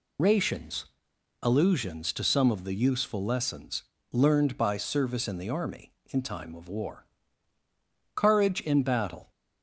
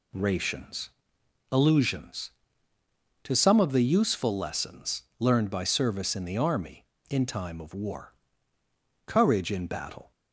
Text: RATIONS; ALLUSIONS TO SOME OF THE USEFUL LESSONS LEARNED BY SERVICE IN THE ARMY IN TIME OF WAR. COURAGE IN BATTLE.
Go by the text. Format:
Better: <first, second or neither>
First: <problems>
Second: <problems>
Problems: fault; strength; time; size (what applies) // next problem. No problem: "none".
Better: second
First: loses the start of "RATIONS"; at 0.1 s; 75 ms // pauses between "LESSONS" and "LEARNED"; slight; at 3.8 s; 0.26 s long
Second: pauses between "LESSONS" and "LEARNED"; slight; at 5.0 s; 0.18 s long